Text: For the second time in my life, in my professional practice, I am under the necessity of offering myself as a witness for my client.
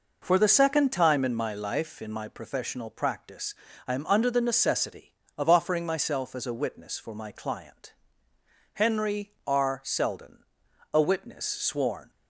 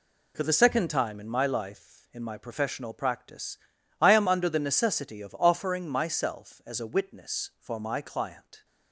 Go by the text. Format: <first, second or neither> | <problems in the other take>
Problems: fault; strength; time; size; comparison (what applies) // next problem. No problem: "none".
second | goes on to say "HENRY R SELDEN a witness sworn"; strong; from 8.7 s on; 3.3 s long